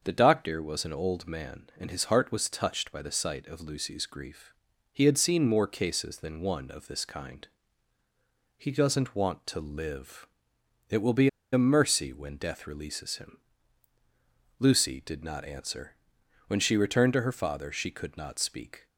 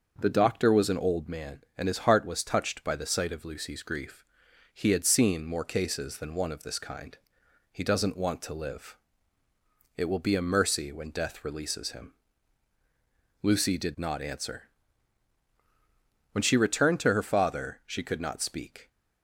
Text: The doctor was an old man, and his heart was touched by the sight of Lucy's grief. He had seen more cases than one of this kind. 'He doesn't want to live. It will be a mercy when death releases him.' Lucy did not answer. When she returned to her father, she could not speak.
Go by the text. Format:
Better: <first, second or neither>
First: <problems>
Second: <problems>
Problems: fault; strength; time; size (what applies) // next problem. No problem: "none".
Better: second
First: starts louder than the rest; until 1.0 s; 6.5 dB // pauses between "be" and "a"; slight; at 11.2 s; 0.24 s long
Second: starts louder than the rest; until 1.2 s; 6 dB